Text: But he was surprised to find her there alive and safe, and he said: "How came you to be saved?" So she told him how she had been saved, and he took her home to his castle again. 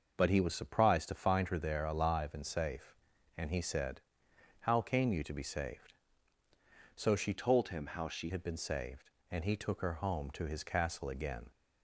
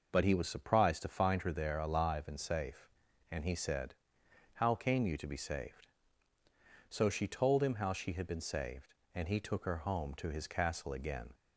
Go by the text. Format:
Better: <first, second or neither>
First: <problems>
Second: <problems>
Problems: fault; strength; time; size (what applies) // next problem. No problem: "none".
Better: second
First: starts louder than the rest; noticeable; until 1.2 s; 6 dB // changes voice from "told" to "she"; from 7.3 to 8.2 s; 0.9 s long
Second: none